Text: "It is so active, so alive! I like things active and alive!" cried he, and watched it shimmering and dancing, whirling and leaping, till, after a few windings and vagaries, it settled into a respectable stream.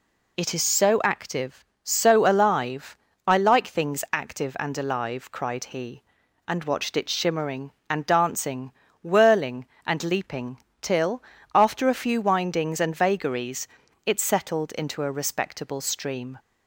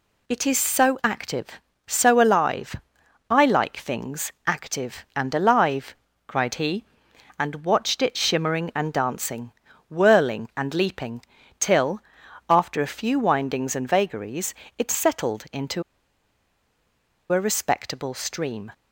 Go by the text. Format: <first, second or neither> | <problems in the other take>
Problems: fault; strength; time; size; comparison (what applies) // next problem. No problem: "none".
first | pauses between "things" and "active"; slight; at 4.3 s; 0.16 s long // pauses between "into" and "a"; strong; at 15.8 s; 1.5 s long